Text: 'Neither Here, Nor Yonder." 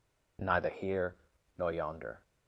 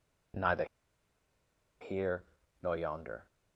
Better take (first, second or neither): first